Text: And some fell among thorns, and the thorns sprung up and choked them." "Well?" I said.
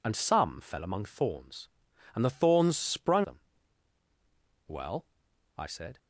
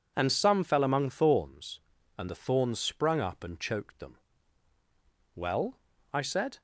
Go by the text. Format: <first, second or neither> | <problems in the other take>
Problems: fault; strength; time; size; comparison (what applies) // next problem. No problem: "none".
second | skips "up and choked"; at 3.2 s